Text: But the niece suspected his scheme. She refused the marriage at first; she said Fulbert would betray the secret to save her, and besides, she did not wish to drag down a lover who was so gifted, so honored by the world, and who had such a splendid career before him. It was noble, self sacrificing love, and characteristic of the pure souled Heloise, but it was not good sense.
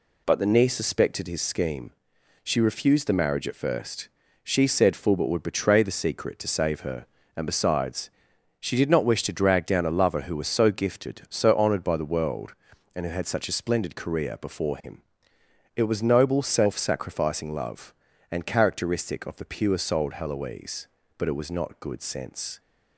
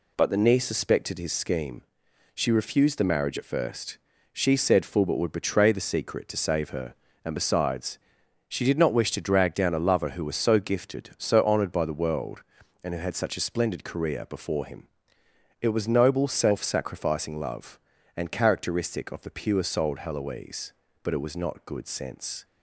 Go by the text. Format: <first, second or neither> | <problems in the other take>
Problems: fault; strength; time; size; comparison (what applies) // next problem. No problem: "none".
neither | none